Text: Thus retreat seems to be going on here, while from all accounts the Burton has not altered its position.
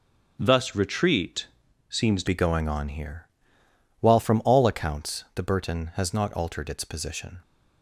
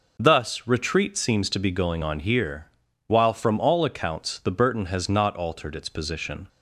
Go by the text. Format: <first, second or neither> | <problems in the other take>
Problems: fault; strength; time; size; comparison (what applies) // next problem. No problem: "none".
second | starts louder than the rest; until 1.4 s; 6 dB // pauses between "retreat" and "seems"; at 1.4 s; 0.42 s long // changes voice at "be"; from 2.2 s on; 5.1 s long